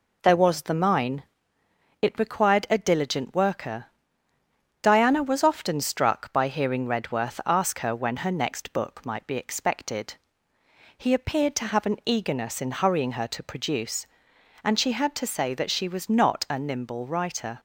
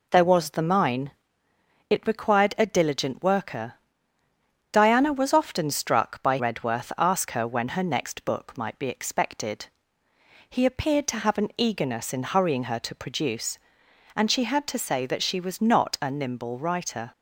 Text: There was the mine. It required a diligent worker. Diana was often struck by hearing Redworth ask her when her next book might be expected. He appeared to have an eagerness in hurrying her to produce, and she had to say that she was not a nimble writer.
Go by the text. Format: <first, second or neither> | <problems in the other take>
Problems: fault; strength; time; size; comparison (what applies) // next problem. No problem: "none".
first | skips "hearing"; at 6.3 s